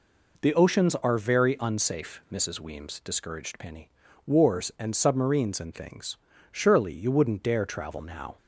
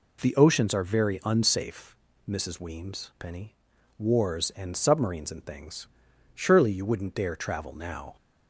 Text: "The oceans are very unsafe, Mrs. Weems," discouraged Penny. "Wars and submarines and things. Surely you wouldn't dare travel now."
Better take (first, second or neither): first